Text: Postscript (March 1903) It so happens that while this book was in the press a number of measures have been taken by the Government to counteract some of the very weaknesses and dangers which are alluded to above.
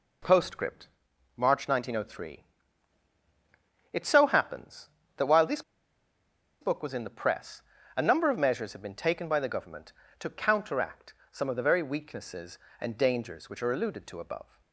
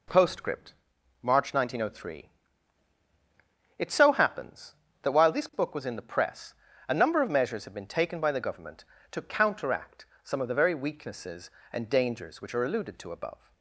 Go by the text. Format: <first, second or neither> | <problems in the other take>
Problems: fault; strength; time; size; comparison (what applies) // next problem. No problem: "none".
second | pauses between "this" and "book"; at 5.6 s; 0.99 s long // pauses between "press" and "a"; slight; at 7.6 s; 0.34 s long; slight in the second // pauses between "counteract" and "some"; slight; at 11.1 s; 0.18 s long; slight in the second